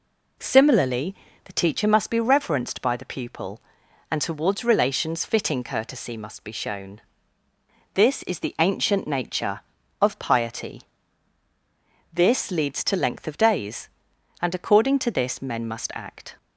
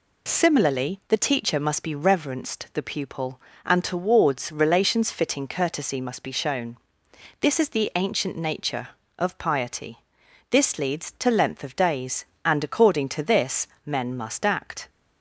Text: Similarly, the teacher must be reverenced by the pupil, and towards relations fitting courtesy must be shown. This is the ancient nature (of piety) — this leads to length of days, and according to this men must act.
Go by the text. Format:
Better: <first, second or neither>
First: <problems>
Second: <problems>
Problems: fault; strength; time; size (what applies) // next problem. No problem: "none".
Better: first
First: none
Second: skips "by"; at 2.6 s // pauses between "this" and "men"; slight; at 13.6 s; 0.16 s long